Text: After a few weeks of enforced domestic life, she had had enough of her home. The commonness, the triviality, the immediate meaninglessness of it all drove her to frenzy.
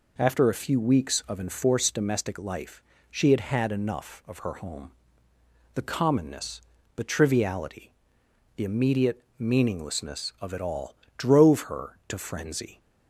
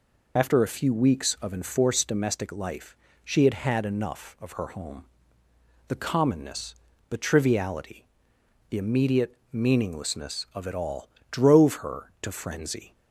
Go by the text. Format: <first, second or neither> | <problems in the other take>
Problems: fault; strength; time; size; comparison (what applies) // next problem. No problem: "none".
first | loses the start of "After"; at 0.3 s; 40 ms // pauses between "immediate" and "meaninglessness"; slight; at 9.3 s; 0.16 s long; slight in the first // pauses between "all" and "drove"; slight; at 11.0 s; 0.24 s long; slight in the first